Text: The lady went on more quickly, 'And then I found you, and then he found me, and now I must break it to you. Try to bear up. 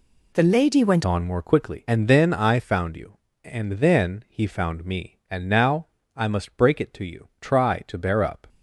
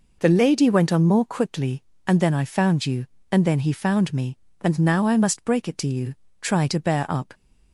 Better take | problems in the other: second | changes voice at "on"; from 1.0 s on; 7.4 s long // pauses between "now" and "I"; slight; at 5.8 s; 0.30 s long

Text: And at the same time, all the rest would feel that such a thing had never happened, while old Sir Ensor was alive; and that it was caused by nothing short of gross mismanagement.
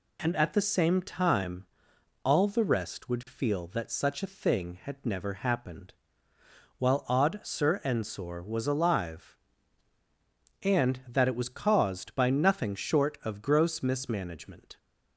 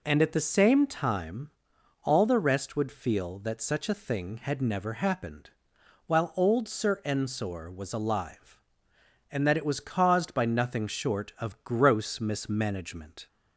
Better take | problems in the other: second | says "odd" for "old"; at 7.0 s

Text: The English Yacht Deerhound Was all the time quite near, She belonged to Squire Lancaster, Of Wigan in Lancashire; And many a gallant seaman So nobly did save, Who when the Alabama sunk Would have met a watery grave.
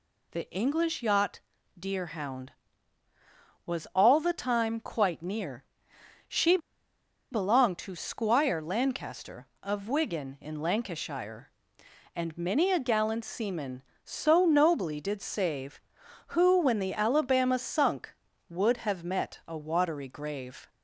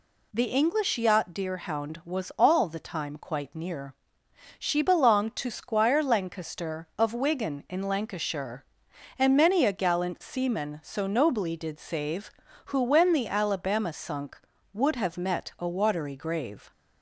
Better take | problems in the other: second | pauses between "Yacht" and "Deerhound"; at 1.3 s; 0.40 s long // pauses between "She" and "belonged"; noticeable; at 6.5 s; 0.74 s long

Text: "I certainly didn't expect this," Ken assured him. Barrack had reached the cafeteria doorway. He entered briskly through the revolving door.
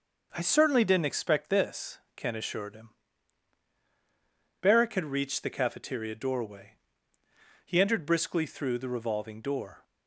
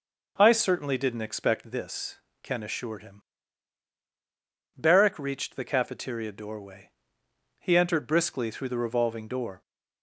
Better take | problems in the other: first | skips "had"; at 5.1 s

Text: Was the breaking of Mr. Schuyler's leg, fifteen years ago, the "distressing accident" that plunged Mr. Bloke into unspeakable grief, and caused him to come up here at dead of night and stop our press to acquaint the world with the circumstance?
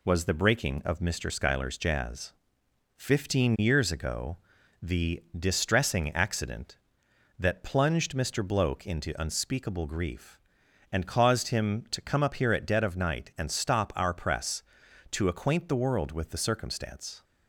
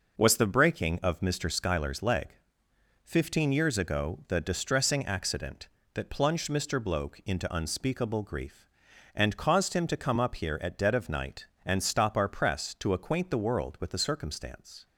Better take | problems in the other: second | says "jazz" for "leg"; at 1.7 s

